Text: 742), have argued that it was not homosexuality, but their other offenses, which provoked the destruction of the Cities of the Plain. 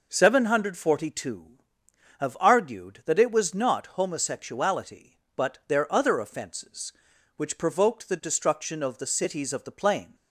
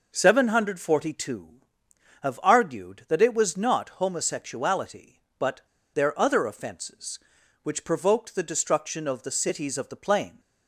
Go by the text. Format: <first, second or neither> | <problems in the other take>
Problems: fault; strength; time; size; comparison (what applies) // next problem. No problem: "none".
first | pauses between "but" and "their"; slight; at 5.6 s; 0.31 s long